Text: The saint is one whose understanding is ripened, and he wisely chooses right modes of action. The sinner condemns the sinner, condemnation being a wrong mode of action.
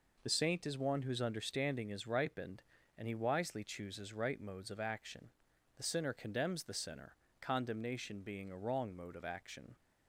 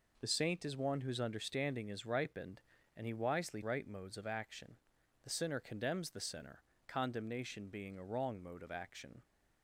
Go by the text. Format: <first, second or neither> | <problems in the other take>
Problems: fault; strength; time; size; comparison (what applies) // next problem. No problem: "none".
first | skips "chooses"; at 3.6 s